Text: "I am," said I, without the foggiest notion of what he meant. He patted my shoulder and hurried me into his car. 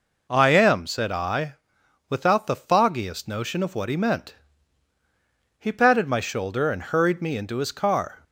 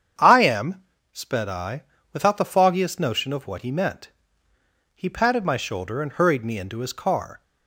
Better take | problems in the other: first | starts louder than the rest; strong; until 1.4 s; 8 dB // says "sped" for "said"; at 1.1 s

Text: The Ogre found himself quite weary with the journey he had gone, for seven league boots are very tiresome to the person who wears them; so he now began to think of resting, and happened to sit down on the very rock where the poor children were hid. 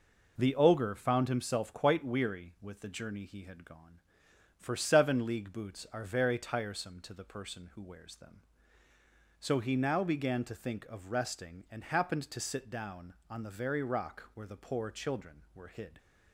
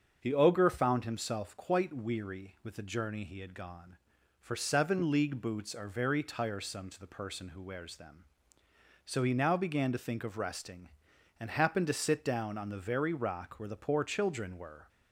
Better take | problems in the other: first | starts louder than the rest; until 1.2 s; 7 dB // stops before "hid"; at 14.8 s

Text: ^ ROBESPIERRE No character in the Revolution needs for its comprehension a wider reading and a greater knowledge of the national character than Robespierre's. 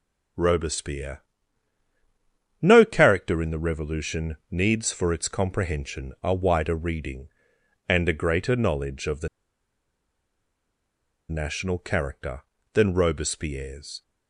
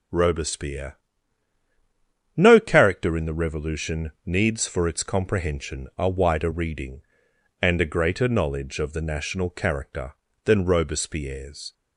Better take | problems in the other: second | pauses between "ROBESPIERRE" and "No"; strong; at 1.2 s; 1.4 s long; strong in the second // pauses between "the" and "national"; strong; at 9.2 s; 2.0 s long

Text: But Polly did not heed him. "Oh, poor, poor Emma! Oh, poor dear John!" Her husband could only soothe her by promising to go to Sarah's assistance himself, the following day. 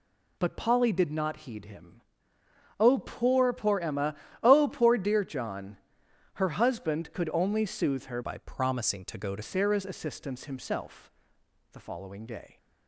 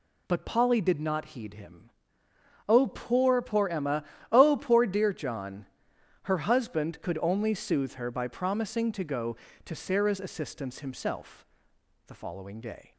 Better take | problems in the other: second | changes voice from "by" to "to"; from 8.2 to 9.4 s; 1.2 s long

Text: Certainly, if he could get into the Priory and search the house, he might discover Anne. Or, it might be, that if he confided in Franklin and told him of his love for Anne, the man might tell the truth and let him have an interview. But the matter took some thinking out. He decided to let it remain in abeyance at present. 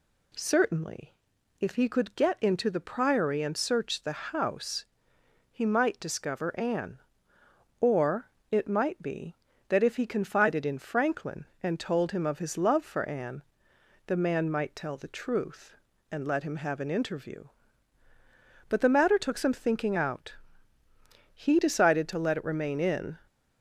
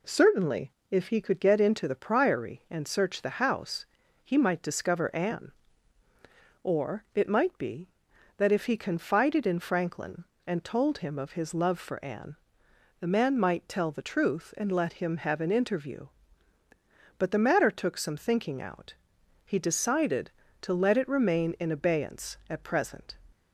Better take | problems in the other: second | stops before "abeyance at present"; at 23.2 s

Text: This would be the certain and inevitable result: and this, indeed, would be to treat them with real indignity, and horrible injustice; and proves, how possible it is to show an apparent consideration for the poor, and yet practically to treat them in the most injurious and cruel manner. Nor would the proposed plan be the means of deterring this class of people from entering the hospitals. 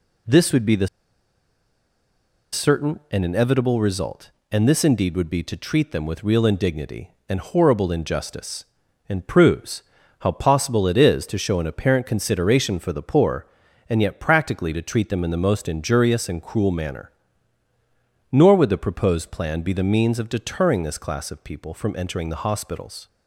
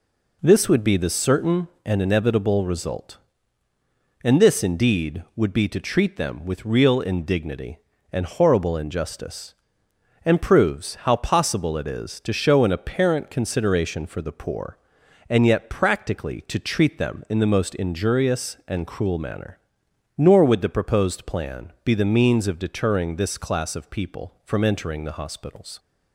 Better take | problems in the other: second | pauses between "the" and "certain"; strong; at 0.8 s; 1.6 s long

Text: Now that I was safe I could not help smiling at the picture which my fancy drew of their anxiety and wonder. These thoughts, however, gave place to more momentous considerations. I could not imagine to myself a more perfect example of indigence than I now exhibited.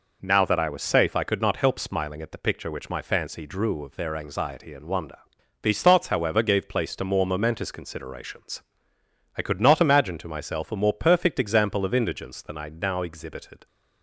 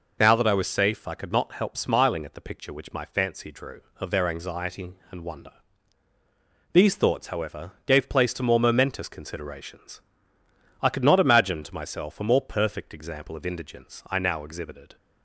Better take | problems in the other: first | skips "than"; at 14.0 s

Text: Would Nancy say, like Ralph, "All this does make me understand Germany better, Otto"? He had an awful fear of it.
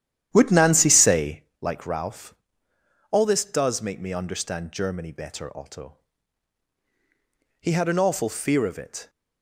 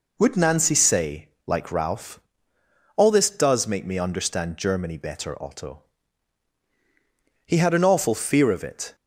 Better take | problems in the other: second | starts louder than the rest; strong; until 1.5 s; 11 dB

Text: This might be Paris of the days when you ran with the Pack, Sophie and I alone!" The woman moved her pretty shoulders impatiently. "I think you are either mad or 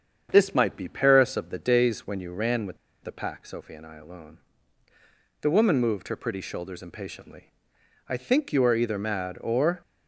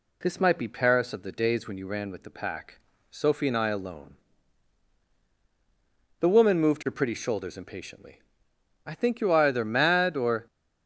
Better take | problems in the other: second | starts louder than the rest; strong; until 1.3 s; 7.5 dB // pauses between "with" and "the"; slight; at 2.7 s; 0.25 s long

